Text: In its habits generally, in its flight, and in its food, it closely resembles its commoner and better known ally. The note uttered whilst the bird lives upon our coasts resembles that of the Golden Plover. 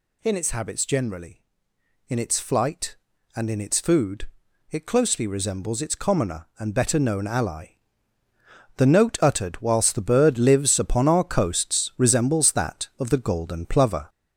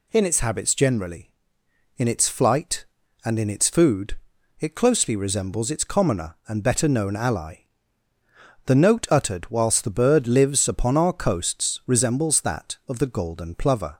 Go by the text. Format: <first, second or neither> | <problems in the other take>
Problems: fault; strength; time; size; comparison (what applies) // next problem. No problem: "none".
second | gets louder; noticeable; throughout; 5 dB